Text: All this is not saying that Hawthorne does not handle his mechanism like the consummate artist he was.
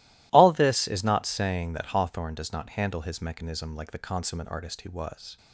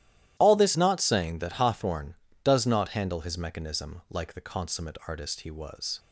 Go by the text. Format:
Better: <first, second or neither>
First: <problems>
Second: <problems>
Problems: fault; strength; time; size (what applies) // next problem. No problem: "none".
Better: first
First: none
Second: starts louder than the rest; strong; until 1.4 s; 13.5 dB // skips "is"; at 0.7 s